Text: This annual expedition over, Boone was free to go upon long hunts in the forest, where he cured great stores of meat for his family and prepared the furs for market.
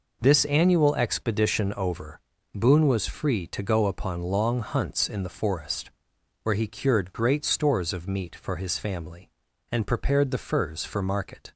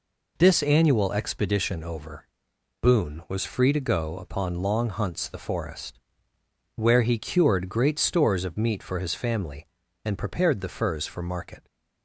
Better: first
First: none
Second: skips "in"; at 5.2 s

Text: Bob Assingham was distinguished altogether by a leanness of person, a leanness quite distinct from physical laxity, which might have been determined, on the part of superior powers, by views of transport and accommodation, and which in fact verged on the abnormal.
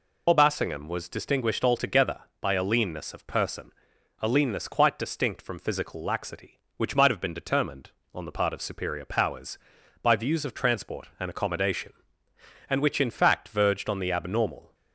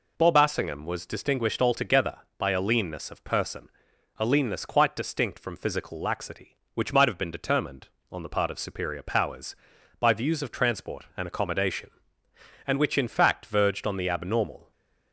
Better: second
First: loses the start of "Bob"; at 0.2 s; 75 ms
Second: none

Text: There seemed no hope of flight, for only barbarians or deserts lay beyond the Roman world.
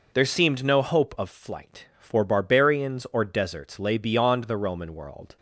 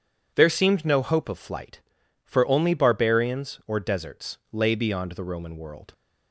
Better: second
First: skips "only"; at 2.2 s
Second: none

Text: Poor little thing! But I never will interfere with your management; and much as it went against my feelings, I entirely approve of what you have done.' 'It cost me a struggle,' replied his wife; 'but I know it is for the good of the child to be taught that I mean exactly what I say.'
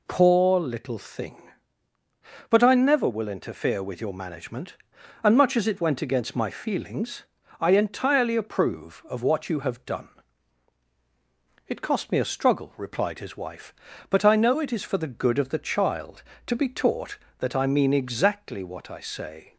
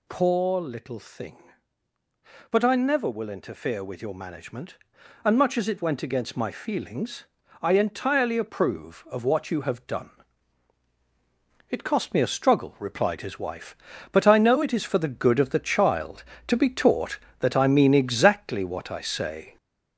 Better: first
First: none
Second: gets louder; noticeable; throughout; 5 dB

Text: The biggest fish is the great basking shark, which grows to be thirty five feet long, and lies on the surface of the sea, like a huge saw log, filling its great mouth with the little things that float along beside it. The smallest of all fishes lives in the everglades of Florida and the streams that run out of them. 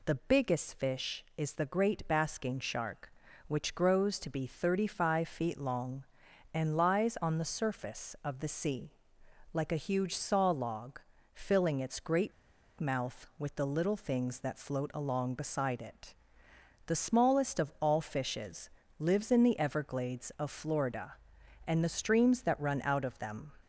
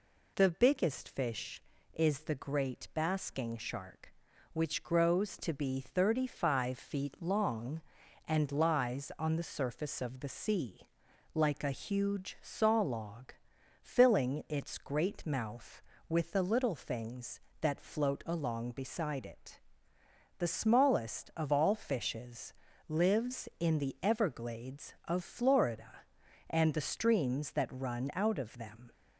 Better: second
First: pauses between "great" and "mouth"; noticeable; at 12.3 s; 0.48 s long // pauses between "fishes" and "lives"; slight; at 18.7 s; 0.28 s long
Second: pauses between "fishes" and "lives"; slight; at 22.5 s; 0.36 s long

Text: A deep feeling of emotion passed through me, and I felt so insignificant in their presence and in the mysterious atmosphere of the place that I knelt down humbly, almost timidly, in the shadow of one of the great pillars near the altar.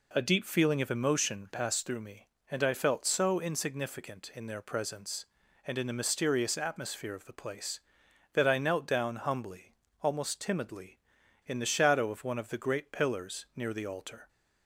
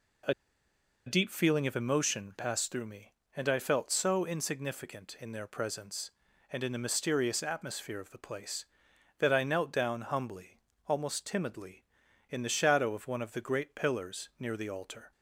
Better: first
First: none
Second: pauses between "A" and "deep"; noticeable; at 0.3 s; 0.73 s long

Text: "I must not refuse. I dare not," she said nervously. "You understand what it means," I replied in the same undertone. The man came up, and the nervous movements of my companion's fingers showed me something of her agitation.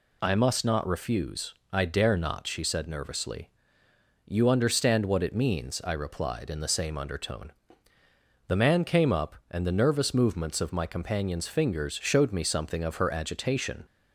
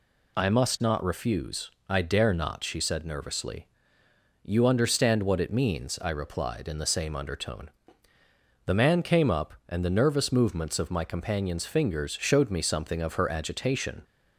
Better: neither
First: none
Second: none

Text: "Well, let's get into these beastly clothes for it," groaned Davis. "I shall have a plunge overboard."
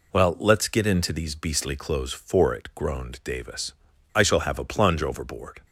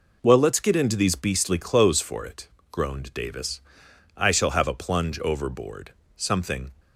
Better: first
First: none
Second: goes on to say "Something"; from 6.1 s on; 0.56 s long

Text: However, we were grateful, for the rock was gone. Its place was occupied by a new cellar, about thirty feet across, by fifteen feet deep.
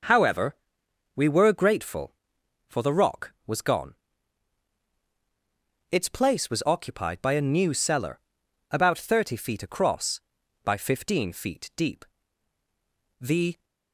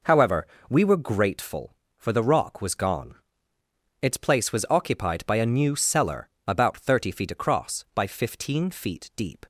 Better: second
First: goes on to say "The"; slight; from 13.2 s on; 0.42 s long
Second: none

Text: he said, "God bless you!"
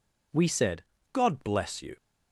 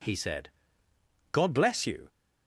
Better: second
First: says "we" for "he"; at 0.3 s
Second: none

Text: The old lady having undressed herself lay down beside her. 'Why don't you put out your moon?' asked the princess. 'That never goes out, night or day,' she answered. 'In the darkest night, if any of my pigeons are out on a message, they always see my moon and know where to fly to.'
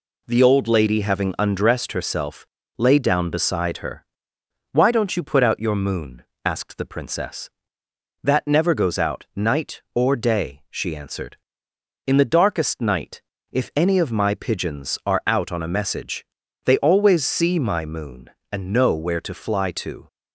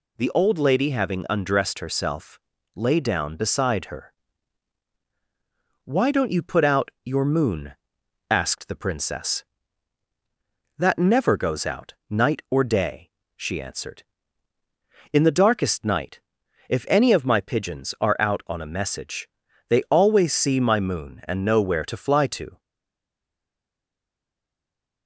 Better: first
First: pauses between "herself" and "lay"; slight; at 2.4 s; 0.32 s long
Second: pauses between "herself" and "lay"; slight; at 2.3 s; 0.36 s long // stays silent after the last word; from 22.5 s on; 2.5 s long

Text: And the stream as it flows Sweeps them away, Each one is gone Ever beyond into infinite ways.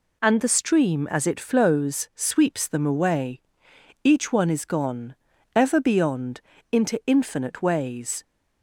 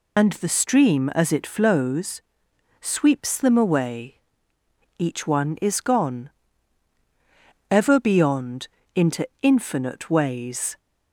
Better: first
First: pauses between "gone" and "Ever"; at 5.1 s; 0.40 s long // pauses between "beyond" and "into"; slight; at 6.4 s; 0.30 s long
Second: loses the start of "And"; at 0.1 s; 55 ms // pauses between "flows" and "Sweeps"; noticeable; at 2.2 s; 0.58 s long // pauses between "gone" and "Ever"; strong; at 6.2 s; 1.4 s long // pauses between "beyond" and "into"; slight; at 8.6 s; 0.28 s long

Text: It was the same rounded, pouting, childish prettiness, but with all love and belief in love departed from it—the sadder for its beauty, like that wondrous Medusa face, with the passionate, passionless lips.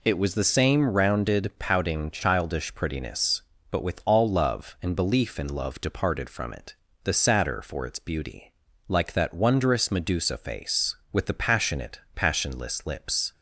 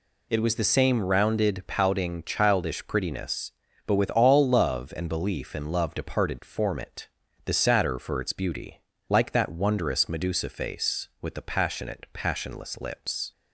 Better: first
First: none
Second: says "form" for "from"; at 6.4 s

